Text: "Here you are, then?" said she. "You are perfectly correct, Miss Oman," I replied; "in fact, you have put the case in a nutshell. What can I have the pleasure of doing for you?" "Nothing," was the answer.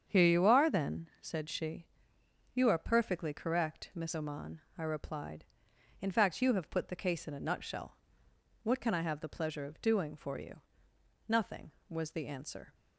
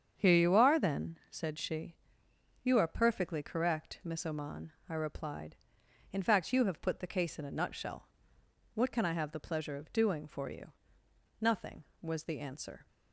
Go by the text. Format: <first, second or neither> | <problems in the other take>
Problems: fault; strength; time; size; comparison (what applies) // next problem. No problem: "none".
neither | starts louder than the rest; strong; the same in both